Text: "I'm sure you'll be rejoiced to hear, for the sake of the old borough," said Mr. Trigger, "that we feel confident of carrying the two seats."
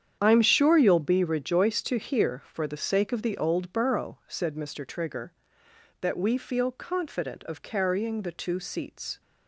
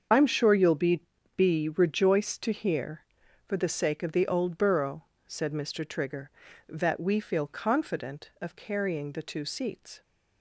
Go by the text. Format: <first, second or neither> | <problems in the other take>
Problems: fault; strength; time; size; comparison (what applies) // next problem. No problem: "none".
first | starts louder than the rest; strong; until 1.4 s; 7 dB; strong in the first // says "be" twice; at 1.3 s